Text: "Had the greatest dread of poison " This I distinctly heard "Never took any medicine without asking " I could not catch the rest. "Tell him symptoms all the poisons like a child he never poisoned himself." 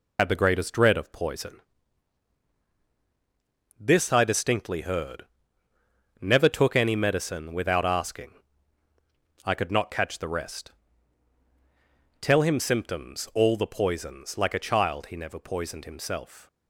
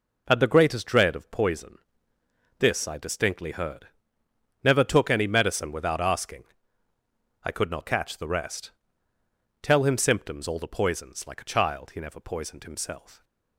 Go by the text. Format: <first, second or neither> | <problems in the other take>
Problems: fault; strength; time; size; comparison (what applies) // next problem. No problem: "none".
second | loses the start of "Had"; at 0.1 s; 75 ms // pauses between "heard" and "Never"; noticeable; at 5.2 s; 0.96 s long; noticeable in the second